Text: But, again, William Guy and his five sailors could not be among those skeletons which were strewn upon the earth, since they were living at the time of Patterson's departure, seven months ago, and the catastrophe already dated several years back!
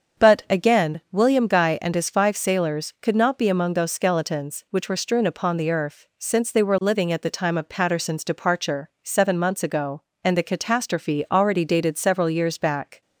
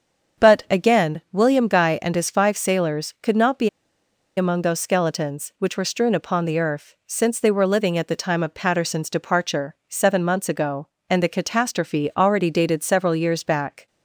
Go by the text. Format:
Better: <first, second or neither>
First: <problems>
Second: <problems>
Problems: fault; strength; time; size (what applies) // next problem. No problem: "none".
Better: first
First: starts louder than the rest; until 1.3 s; 7 dB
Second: starts louder than the rest; until 1.5 s; 7 dB // pauses between "be" and "among"; noticeable; at 3.6 s; 0.68 s long